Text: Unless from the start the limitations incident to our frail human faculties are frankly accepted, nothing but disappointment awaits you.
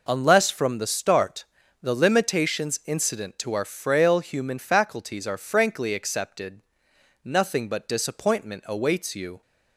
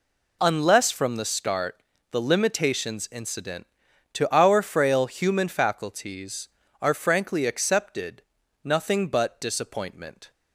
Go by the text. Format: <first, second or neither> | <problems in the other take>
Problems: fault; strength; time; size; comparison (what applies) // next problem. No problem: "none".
first | pauses between "start" and "the"; slight; at 1.7 s; 0.32 s long; also in the first // stops before "awaits you"; at 10.3 s